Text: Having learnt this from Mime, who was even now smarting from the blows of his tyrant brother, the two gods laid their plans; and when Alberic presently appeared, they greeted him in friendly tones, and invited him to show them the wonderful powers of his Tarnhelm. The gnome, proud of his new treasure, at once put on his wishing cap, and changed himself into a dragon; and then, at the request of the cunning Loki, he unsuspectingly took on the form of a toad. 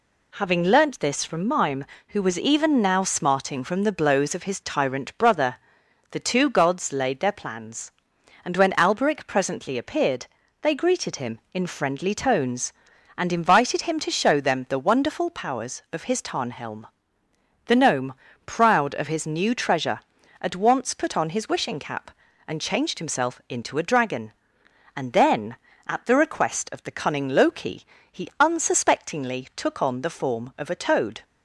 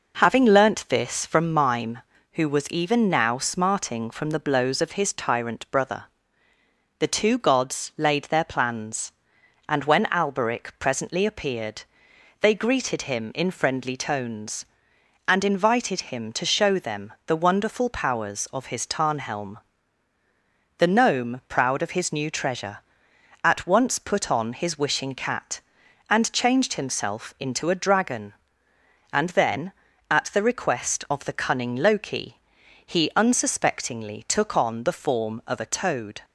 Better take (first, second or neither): first